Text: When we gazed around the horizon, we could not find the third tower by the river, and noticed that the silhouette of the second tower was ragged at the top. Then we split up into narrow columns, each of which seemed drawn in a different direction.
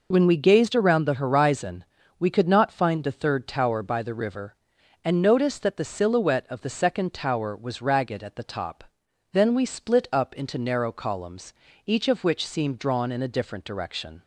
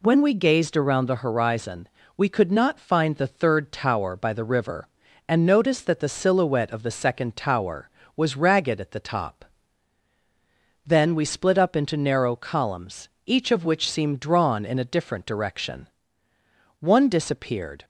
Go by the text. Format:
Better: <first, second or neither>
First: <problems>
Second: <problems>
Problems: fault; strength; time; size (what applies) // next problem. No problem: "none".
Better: first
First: none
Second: goes on to say "One disappeared"; noticeable; from 16.8 s on; 1.0 s long